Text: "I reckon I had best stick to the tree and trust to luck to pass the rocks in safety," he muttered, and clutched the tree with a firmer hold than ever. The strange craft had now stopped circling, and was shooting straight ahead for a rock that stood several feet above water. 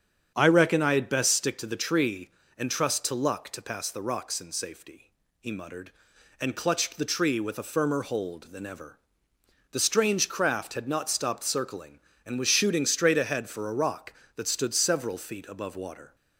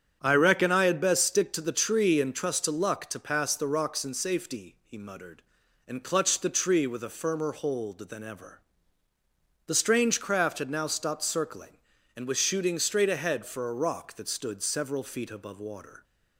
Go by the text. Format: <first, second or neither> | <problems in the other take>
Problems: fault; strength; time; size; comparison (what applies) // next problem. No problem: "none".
second | starts louder than the rest; strong; until 1.3 s; 8 dB; strong in the second // says "not" for "now"; at 10.8 s